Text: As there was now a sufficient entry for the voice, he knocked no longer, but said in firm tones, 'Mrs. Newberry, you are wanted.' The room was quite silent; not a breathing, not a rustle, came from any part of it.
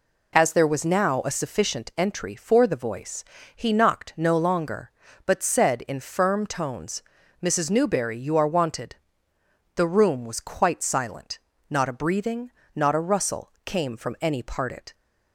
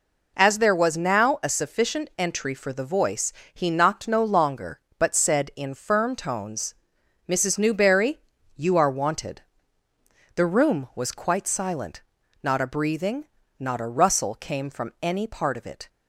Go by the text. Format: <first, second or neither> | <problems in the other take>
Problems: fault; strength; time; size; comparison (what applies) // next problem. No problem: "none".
second | skips "of"; at 14.7 s